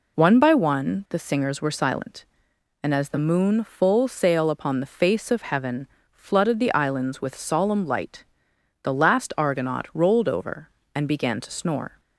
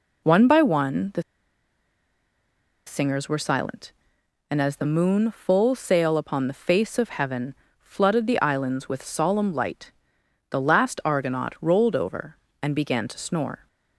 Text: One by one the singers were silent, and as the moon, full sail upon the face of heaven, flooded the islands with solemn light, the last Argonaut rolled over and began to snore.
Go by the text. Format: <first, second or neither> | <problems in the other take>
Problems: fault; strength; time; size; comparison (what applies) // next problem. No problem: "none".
first | pauses between "the" and "singers"; strong; at 1.2 s; 1.6 s long